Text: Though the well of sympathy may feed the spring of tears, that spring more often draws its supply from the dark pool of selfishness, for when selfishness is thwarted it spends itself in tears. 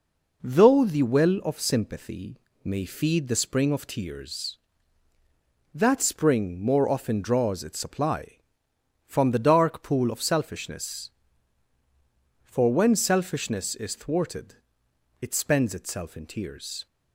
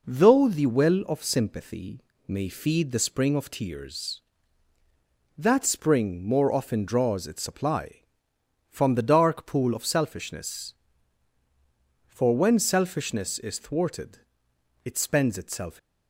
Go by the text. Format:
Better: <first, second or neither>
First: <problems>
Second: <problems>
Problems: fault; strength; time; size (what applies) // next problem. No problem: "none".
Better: first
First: pauses between "sympathy" and "may"; slight; at 2.3 s; 0.26 s long // pauses between "thwarted" and "it"; noticeable; at 14.5 s; 0.66 s long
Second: pauses between "sympathy" and "may"; slight; at 2.0 s; 0.26 s long // pauses between "thwarted" and "it"; noticeable; at 14.1 s; 0.66 s long // stops before "in tears"; at 15.7 s